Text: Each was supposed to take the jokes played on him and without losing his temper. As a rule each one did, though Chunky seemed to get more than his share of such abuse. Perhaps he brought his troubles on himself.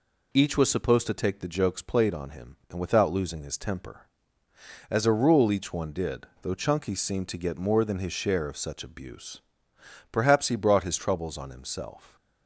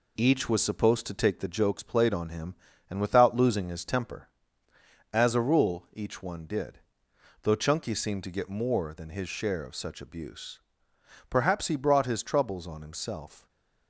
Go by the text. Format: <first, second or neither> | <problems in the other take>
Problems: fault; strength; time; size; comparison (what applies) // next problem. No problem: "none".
first | gets quieter; noticeable; throughout; 4 dB // stays silent after the last word; slight; from 13.3 s on; 0.5 s long